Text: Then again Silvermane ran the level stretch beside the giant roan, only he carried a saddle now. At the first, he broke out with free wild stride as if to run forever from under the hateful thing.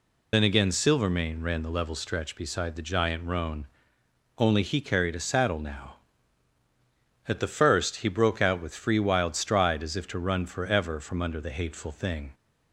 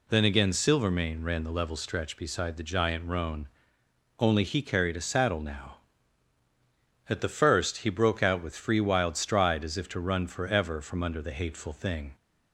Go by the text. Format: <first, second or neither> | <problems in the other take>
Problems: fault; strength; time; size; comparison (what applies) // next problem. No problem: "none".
second | loses the start of "Then"; at 0.3 s; 50 ms